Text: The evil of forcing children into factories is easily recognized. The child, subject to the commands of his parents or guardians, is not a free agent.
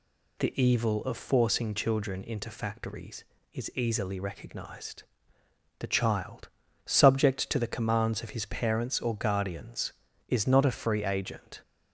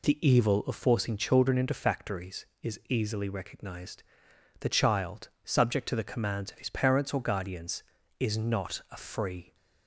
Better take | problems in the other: first | stops before "agent"; at 9.5 s

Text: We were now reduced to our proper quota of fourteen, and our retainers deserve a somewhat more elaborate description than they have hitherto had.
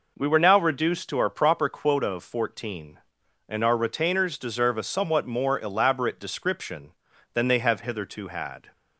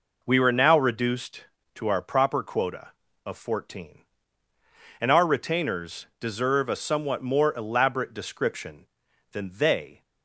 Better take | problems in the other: first | stops before "have hitherto had"; at 10.0 s

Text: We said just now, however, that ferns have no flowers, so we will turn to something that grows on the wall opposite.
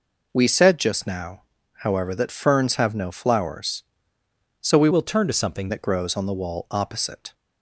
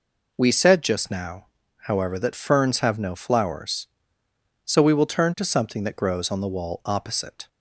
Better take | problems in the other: second | changes voice from "will" to "something"; from 4.9 to 5.6 s; 0.7 s long

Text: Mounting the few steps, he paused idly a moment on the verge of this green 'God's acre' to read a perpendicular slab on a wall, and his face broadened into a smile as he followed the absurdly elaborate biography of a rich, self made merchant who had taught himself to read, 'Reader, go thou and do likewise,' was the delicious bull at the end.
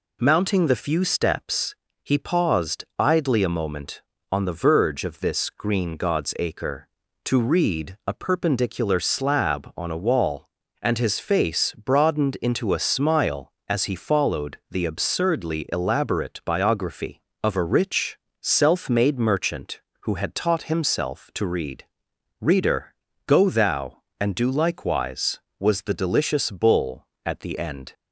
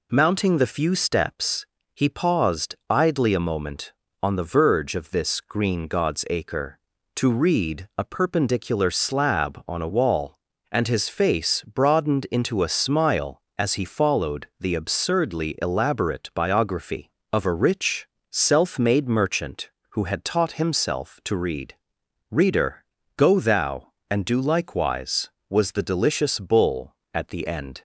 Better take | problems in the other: neither | none

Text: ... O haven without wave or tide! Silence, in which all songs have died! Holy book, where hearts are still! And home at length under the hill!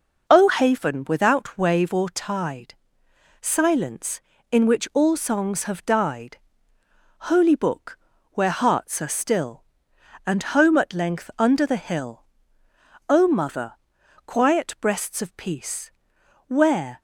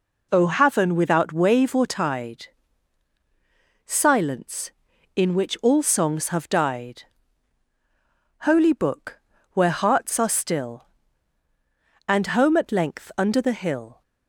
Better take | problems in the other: second | goes on to say "O mother quiet breasts of peace Where"; strong; from 13.0 s on; 3.9 s long

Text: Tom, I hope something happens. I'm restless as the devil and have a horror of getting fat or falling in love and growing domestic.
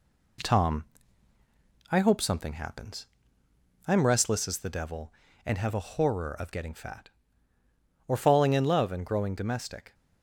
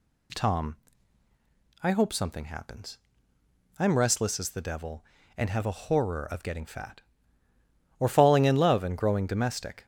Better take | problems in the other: second | gets quieter; slight; throughout; 2.5 dB

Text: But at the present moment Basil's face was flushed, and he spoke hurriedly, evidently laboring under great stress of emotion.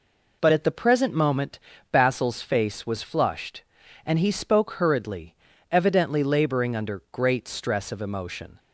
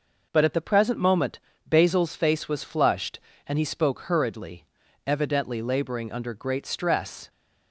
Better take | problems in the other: first | pauses between "moment" and "Basil's"; slight; at 1.3 s; 0.26 s long; slight in the first // stops before "of emotion"; at 7.2 s

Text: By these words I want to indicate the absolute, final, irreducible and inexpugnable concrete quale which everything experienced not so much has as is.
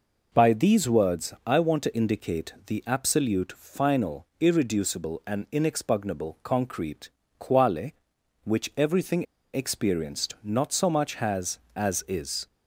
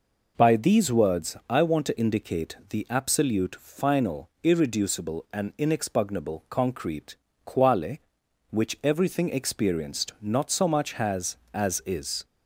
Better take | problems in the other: second | pauses between "concrete" and "quale"; slight; at 7.0 s; 0.28 s long; slight in the second // pauses between "everything" and "experienced"; slight; at 9.2 s; 0.29 s long

